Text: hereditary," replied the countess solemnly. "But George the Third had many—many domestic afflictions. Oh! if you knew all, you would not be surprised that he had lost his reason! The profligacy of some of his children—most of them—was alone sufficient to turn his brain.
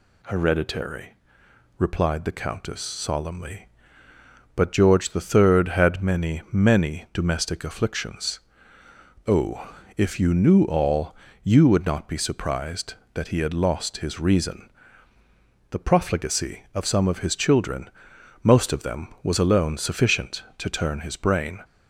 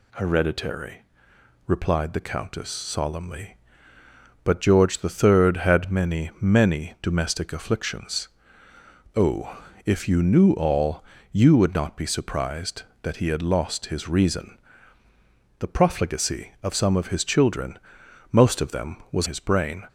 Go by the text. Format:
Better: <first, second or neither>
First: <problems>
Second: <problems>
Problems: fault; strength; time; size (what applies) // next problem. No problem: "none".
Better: first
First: none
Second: skips "alone sufficient to turn"; at 19.2 s